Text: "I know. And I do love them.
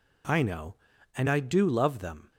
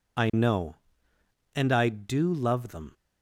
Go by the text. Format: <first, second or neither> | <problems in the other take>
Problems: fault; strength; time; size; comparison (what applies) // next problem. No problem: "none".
neither | none